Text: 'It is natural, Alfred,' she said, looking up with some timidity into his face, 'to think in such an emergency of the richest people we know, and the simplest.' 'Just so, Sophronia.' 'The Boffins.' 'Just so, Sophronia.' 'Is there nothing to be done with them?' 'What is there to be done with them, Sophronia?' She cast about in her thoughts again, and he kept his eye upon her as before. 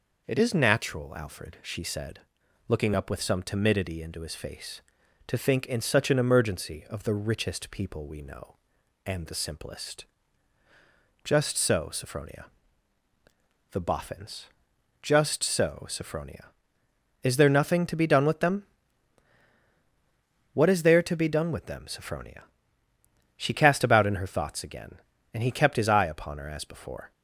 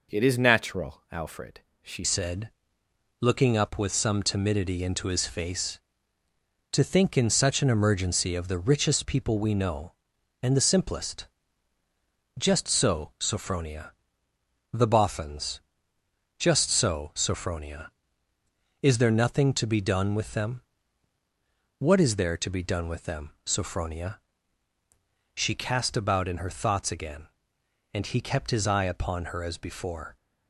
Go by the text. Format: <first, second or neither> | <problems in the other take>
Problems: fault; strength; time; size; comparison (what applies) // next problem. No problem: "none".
first | changes voice at "said"; from 2.0 s on; 28.1 s long